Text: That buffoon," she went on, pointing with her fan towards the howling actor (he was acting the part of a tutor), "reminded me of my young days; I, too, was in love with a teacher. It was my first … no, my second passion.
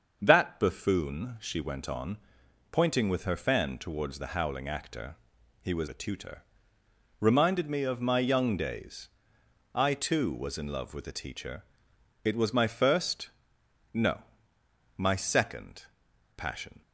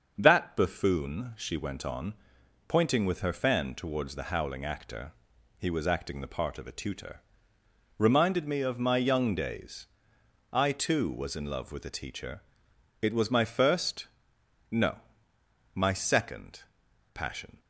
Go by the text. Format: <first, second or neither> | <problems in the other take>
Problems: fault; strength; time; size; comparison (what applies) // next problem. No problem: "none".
second | starts louder than the rest; until 1.2 s; 6.5 dB; also in the second // skips "acting the part of"; at 5.8 s // pauses between "second" and "passion"; noticeable; at 15.8 s; 0.52 s long; noticeable in the second